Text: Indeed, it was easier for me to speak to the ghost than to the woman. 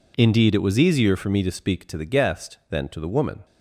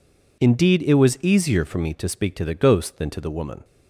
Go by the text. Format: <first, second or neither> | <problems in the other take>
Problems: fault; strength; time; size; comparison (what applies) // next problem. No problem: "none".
second | says "guest" for "ghost"; at 2.0 s